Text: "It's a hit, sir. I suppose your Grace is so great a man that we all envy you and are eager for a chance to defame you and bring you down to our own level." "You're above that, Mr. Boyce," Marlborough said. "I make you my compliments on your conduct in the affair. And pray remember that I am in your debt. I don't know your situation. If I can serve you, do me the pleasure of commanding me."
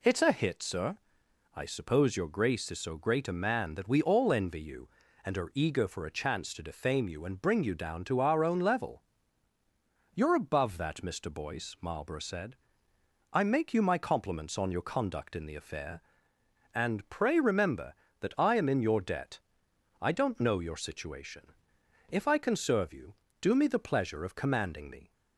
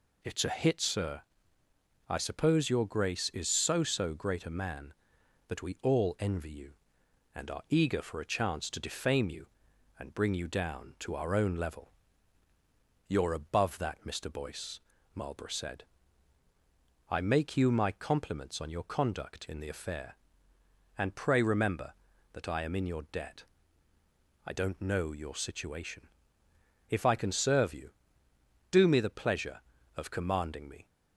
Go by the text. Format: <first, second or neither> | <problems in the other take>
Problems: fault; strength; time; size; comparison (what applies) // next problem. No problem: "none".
first | says "so" twice; at 3.8 s